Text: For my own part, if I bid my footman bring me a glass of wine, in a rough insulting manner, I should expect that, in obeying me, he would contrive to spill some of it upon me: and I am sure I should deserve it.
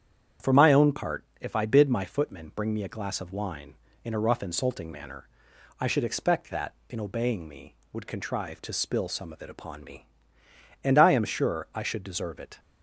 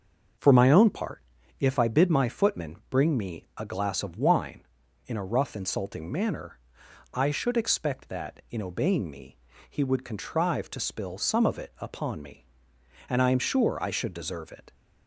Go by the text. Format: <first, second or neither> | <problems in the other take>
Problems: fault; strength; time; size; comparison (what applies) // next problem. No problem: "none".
second | starts louder than the rest; strong; until 1.5 s; 8.5 dB; also in the second // skips "he"; at 7.8 s